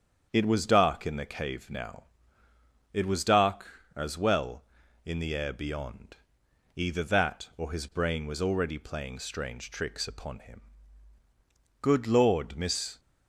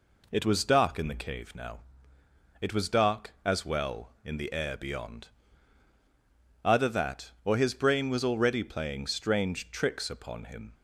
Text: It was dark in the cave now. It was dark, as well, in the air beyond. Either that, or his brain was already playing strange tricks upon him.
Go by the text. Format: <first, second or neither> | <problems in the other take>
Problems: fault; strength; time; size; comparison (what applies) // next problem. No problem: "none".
second | starts louder than the rest; strong; until 1.3 s; 7.5 dB // goes on to say "Good Lord Miss"; noticeable; from 11.8 s on; 1.1 s long